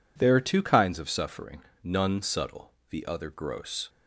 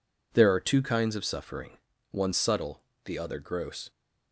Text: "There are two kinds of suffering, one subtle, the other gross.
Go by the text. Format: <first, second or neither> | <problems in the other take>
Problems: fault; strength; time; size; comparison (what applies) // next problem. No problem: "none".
second | says "none" for "one"; at 1.8 s